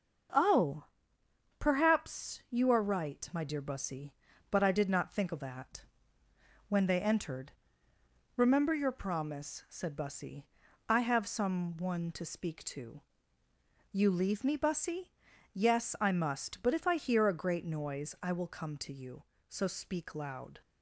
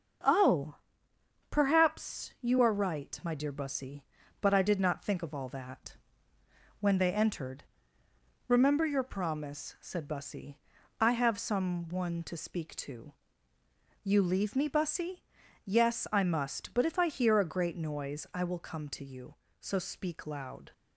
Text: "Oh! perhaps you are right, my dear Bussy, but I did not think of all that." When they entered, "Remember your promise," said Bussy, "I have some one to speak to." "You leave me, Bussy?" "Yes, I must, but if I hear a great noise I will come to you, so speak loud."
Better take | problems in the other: second | starts louder than the rest; until 2.0 s; 6.5 dB; also in the second // skips "all"; at 5.4 s

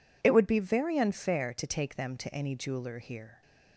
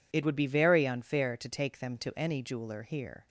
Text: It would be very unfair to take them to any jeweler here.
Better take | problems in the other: neither | none

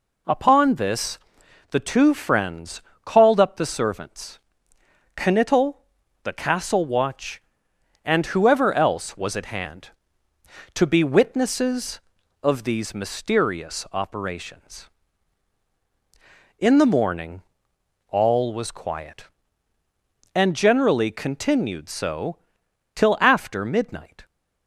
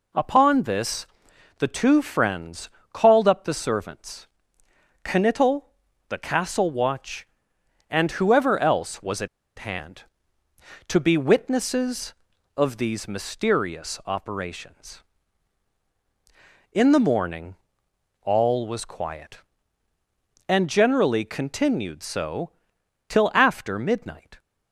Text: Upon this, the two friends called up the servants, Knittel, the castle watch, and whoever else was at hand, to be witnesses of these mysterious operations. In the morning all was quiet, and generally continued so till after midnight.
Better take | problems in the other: first | pauses between "friends" and "called"; slight; at 2.6 s; 0.24 s long; slight in the first // pauses between "at" and "hand"; slight; at 9.2 s; 0.30 s long // pauses between "morning" and "all"; noticeable; at 17.5 s; 0.68 s long; noticeable in the first // pauses between "so" and "till"; noticeable; at 22.4 s; 0.60 s long; noticeable in the first

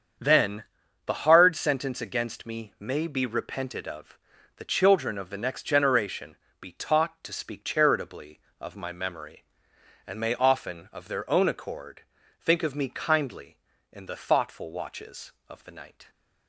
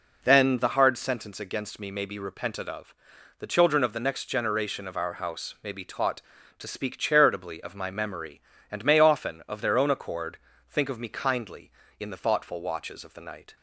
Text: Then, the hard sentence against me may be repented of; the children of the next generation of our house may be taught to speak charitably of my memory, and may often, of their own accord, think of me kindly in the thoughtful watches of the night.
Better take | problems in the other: second | starts louder than the rest; strong; until 1.6 s; 7.5 dB // skips "of our house may"; at 6.4 s

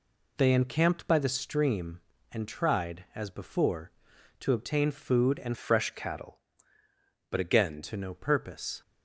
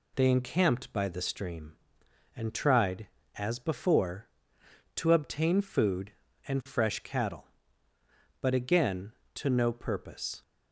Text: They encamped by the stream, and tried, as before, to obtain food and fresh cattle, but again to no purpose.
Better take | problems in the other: second | changes voice from "fresh" to "again"; from 5.5 to 7.8 s; 2.3 s long

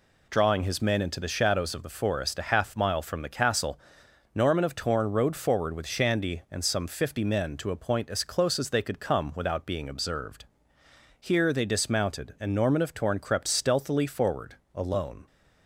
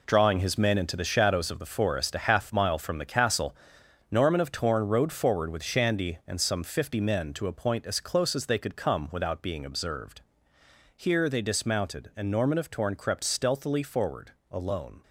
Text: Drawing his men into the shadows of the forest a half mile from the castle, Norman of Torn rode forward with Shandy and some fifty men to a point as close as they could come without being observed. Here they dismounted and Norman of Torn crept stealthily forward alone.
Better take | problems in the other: first | gets quieter; strong; throughout; 9.5 dB // pauses between "forward" and "alone"; slight; at 14.3 s; 0.18 s long; slight in the first

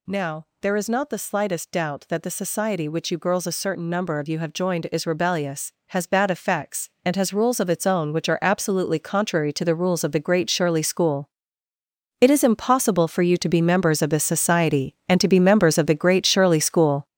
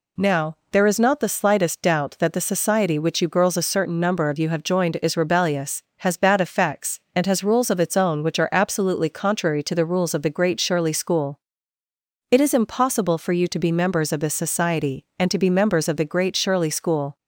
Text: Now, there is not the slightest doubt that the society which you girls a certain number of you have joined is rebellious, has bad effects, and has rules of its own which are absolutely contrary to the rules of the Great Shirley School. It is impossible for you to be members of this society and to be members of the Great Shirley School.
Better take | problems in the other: second | gets louder; strong; throughout; 8 dB

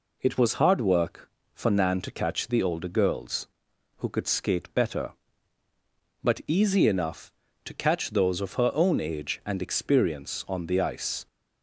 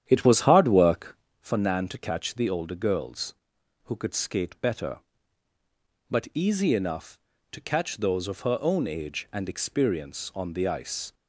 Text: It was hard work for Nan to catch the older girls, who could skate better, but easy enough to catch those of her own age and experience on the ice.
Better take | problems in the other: first | starts louder than the rest; strong; until 1.4 s; 10 dB

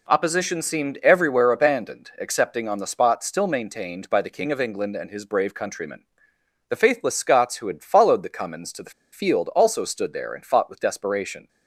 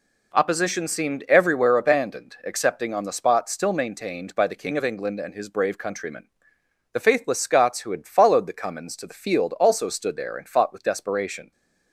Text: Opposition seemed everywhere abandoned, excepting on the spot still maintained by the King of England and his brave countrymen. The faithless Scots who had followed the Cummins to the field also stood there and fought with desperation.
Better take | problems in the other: second | pauses between "the" and "field"; slight; at 8.9 s; 0.21 s long

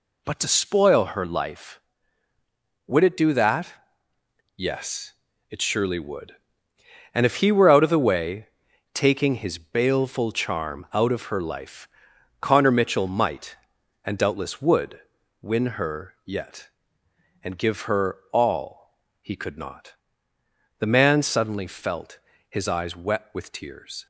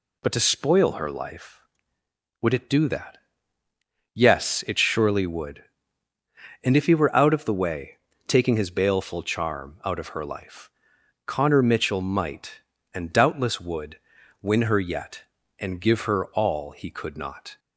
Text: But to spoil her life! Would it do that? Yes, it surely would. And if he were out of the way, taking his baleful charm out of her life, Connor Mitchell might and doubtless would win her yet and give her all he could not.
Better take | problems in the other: second | pauses between "would" and "win"; at 14.9 s; 0.42 s long; also in the second // pauses between "all" and "he"; slight; at 18.9 s; 0.26 s long // goes on to say "The man suddenly felt his eyes wet with tears"; strong; from 20.7 s on; 3.2 s long

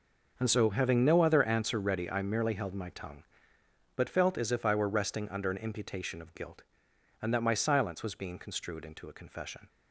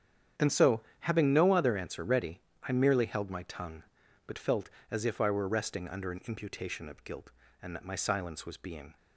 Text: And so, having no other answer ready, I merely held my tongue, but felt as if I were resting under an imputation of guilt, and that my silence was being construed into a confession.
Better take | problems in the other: first | starts louder than the rest; strong; until 1.5 s; 8.5 dB // stops before "construed into a confession"; at 8.9 s

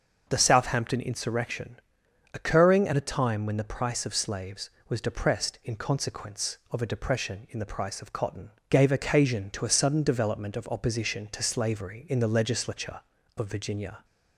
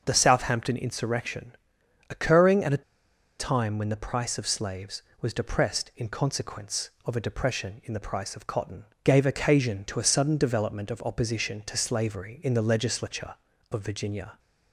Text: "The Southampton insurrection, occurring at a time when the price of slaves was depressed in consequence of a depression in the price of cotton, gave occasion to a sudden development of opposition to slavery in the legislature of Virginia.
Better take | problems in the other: first | starts louder than the rest; until 1.0 s; 6 dB; also in the first // pauses between "a" and "time"; noticeable; at 2.8 s; 0.58 s long

